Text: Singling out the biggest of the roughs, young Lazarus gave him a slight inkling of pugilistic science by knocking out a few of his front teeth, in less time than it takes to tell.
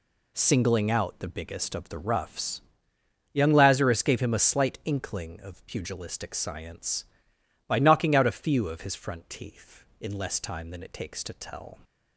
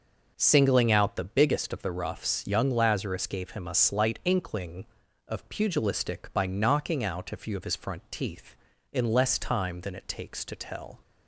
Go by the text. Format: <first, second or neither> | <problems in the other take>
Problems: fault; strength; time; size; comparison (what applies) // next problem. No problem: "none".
first | skips "science"; at 6.3 s